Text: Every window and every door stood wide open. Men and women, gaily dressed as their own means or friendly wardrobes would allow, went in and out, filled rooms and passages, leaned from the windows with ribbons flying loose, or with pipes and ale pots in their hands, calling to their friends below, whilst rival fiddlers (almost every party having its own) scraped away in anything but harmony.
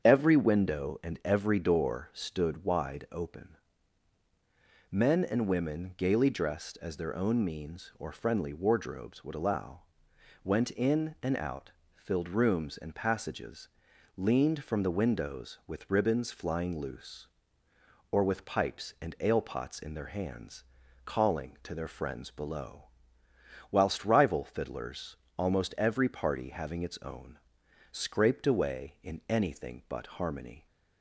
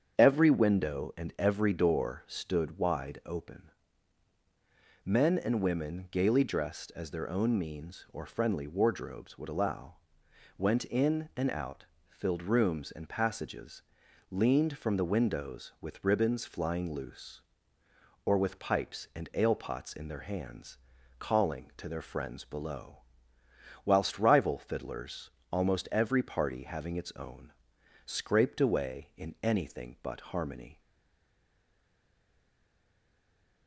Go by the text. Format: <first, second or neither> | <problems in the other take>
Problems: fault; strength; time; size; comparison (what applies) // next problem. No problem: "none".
first | starts louder than the rest; strong; until 1.2 s; 7.5 dB; strong in the first // stays silent after the last word; strong; from 30.7 s on; 2.9 s long